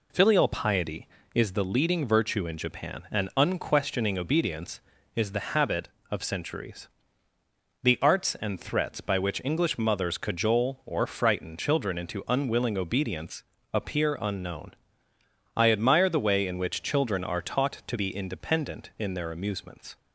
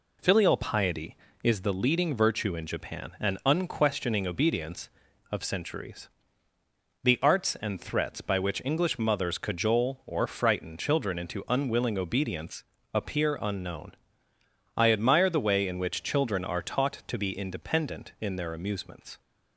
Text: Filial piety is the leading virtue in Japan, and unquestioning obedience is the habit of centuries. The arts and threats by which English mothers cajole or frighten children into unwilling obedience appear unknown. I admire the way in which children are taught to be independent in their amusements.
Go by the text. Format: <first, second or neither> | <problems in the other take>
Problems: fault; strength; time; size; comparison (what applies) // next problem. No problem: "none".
first | skips "is the habit"; at 5.0 s // pauses between "obedience" and "appear"; slight; at 12.6 s; 0.28 s long; slight in the first